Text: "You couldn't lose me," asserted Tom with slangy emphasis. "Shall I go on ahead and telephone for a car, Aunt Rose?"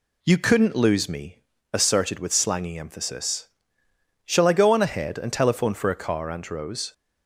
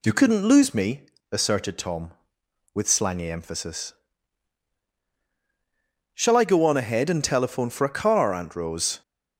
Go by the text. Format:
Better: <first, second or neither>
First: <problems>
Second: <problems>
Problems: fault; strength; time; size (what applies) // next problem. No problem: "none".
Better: second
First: skips "Tom"; at 2.1 s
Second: none